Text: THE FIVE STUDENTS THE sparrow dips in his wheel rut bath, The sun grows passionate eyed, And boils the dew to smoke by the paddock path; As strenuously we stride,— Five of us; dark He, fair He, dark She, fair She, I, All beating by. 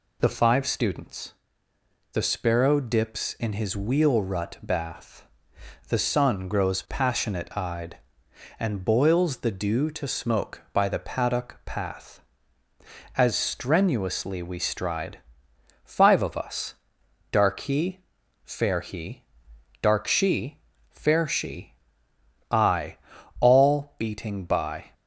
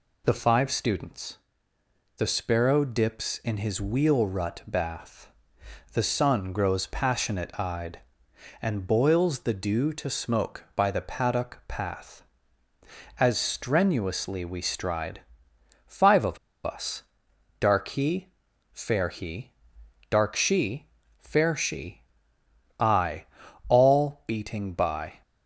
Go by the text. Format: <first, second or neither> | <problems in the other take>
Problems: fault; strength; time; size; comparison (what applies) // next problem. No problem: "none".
first | pauses between "STUDENTS" and "THE"; noticeable; at 1.3 s; 0.80 s long; noticeable in the first // pauses between "of" and "us"; slight; at 16.3 s; 0.27 s long